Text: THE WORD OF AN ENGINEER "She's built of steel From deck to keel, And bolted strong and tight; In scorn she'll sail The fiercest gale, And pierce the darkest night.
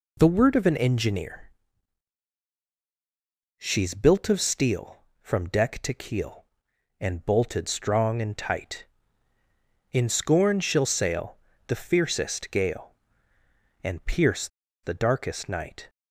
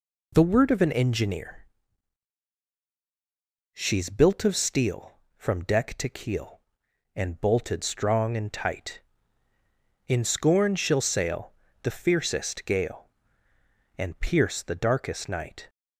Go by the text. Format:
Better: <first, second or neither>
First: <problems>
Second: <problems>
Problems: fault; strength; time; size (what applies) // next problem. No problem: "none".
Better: second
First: pauses between "ENGINEER" and "She's"; strong; at 1.5 s; 2.0 s long // pauses between "sail" and "The"; slight; at 11.3 s; 0.32 s long // pauses between "pierce" and "the"; slight; at 14.4 s; 0.35 s long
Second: pauses between "ENGINEER" and "She's"; strong; at 1.6 s; 2.0 s long // pauses between "sail" and "The"; slight; at 11.5 s; 0.32 s long